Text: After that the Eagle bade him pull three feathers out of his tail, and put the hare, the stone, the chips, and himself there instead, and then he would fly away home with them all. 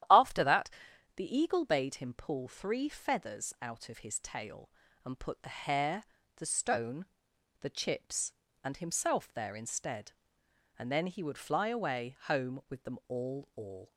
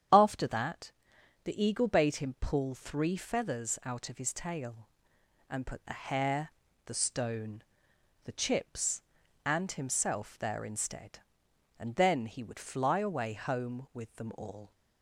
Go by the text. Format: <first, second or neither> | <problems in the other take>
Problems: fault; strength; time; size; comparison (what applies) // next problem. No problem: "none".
second | starts louder than the rest; strong; until 1.5 s; 11.5 dB; strong in the second // pauses between "that" and "the"; noticeable; at 0.6 s; 0.46 s long; noticeable in the second // says "all" twice; at 13.5 s